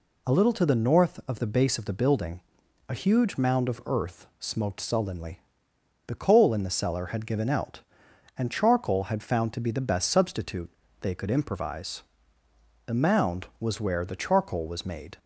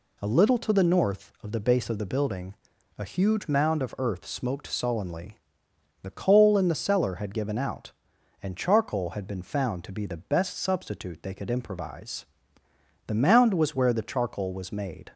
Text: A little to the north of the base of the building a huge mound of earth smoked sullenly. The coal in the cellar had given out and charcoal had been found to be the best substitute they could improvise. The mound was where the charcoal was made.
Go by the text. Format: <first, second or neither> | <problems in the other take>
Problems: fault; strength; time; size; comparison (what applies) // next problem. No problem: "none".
second | pauses between "building" and "a"; noticeable; at 2.3 s; 0.48 s long; also in the second // skips "been"; at 9.2 s // pauses between "substitute" and "they"; slight; at 10.6 s; 0.32 s long